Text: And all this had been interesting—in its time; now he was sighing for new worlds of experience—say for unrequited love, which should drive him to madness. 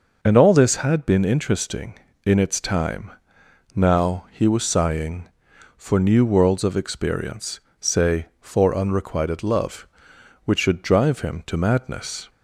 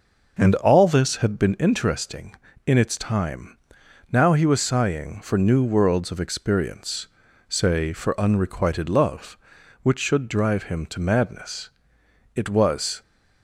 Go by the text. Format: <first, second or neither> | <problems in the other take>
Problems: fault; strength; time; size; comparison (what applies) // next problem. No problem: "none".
first | goes on to say "It was"; noticeable; from 12.3 s on; 0.66 s long